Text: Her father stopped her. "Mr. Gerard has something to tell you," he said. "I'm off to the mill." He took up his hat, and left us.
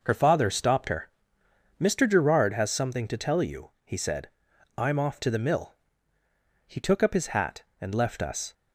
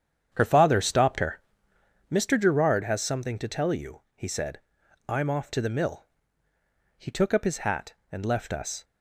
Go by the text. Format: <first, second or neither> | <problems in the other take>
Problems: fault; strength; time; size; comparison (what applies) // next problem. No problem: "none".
first | starts louder than the rest; strong; until 2.0 s; 8.5 dB